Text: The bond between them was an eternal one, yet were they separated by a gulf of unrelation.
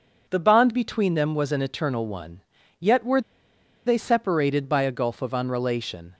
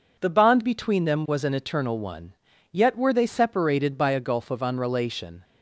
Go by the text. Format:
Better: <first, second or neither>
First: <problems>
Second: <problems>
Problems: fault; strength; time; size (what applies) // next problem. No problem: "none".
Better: second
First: pauses between "were" and "they"; noticeable; at 3.2 s; 0.65 s long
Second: none